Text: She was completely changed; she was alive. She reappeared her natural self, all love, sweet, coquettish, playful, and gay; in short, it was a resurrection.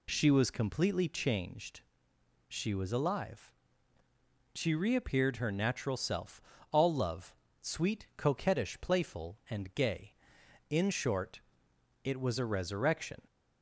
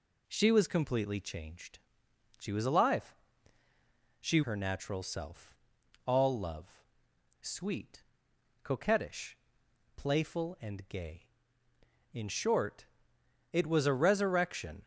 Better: first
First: none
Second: skips "reappeared"; at 4.4 s

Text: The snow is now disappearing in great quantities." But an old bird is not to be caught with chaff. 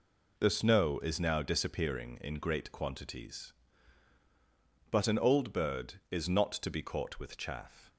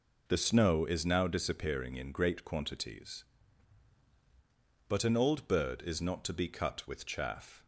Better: first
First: none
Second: says "cut" for "caught"; at 6.4 s

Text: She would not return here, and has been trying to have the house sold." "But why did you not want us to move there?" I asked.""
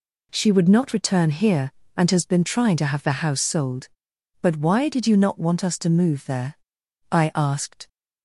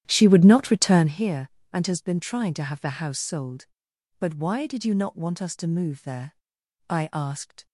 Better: first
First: none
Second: starts louder than the rest; strong; until 1.1 s; 11.5 dB

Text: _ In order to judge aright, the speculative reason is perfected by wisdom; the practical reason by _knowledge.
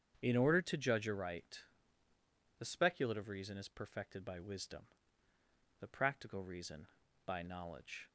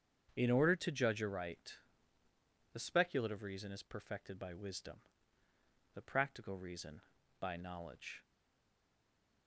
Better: first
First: starts louder than the rest; strong; until 1.2 s; 7.5 dB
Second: starts louder than the rest; strong; until 1.3 s; 7.5 dB // stays silent after the last word; noticeable; from 8.2 s on; 1.2 s long

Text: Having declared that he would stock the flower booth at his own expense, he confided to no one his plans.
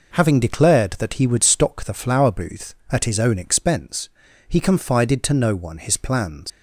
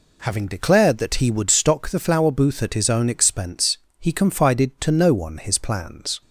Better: second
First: leaves "plans" unfinished; at 6.5 s; 100 ms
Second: none

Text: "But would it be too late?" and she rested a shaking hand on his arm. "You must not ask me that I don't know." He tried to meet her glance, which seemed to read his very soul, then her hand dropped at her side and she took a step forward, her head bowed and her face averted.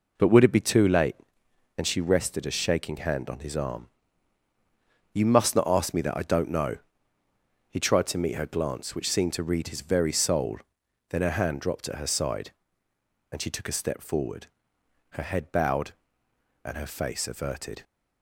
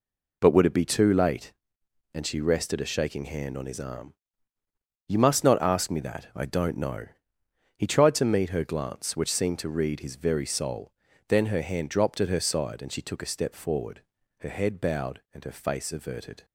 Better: neither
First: none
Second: none

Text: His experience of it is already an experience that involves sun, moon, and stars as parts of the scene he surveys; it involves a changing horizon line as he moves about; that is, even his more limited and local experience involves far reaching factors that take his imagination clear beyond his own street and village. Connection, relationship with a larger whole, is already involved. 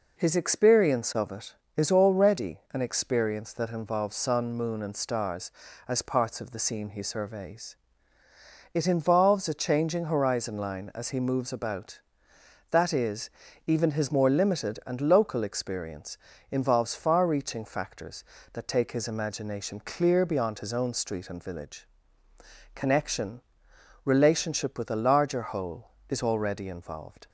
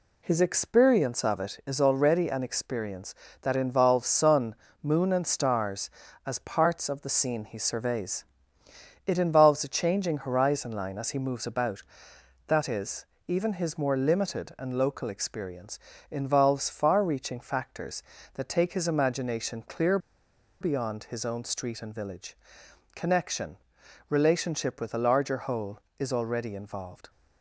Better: first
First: pauses between "experience" and "involves"; slight; at 16.1 s; 0.34 s long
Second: pauses between "experience" and "involves"; slight; at 15.7 s; 0.28 s long // pauses between "clear" and "beyond"; noticeable; at 19.9 s; 0.62 s long

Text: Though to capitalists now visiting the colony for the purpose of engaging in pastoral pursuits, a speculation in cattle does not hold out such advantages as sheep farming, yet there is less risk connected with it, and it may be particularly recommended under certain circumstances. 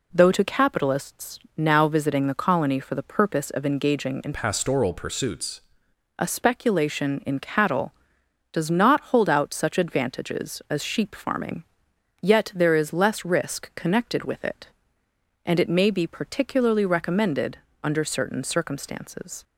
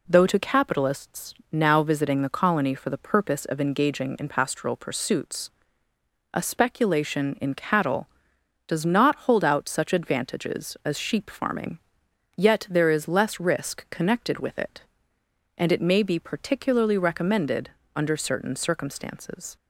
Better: second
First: pauses between "capitalists" and "now"; slight; at 1.3 s; 0.16 s long // changes voice from "pastoral" to "pursuits"; from 4.3 to 5.6 s; 1.3 s long // pauses between "recommended" and "under"; slight; at 17.5 s; 0.26 s long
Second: pauses between "capitalists" and "now"; slight; at 1.3 s; 0.16 s long // pauses between "recommended" and "under"; slight; at 17.6 s; 0.26 s long

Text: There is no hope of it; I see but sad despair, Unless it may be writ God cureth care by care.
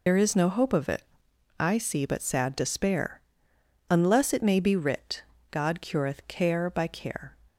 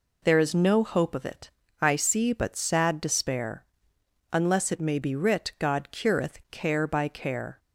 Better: second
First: loses the start of "There"; at 0.0 s; 70 ms // pauses between "writ" and "God"; slight; at 5.2 s; 0.30 s long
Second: none

